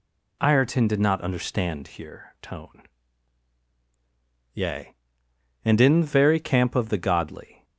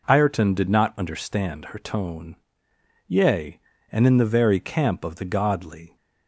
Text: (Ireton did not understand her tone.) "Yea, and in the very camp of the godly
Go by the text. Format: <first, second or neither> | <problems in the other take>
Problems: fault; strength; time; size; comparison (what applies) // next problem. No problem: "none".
second | says "here" for "her"; at 1.8 s